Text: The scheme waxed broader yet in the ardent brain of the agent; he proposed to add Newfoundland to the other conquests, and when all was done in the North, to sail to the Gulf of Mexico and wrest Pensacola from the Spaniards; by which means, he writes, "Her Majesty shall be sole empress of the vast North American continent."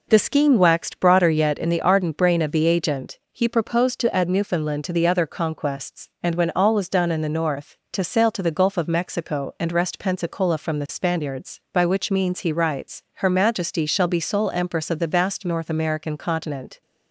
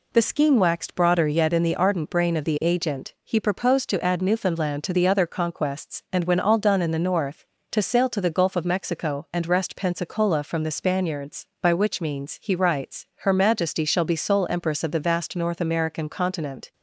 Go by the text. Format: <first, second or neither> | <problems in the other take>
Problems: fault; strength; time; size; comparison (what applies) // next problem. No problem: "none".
first | skips "was"; at 6.5 s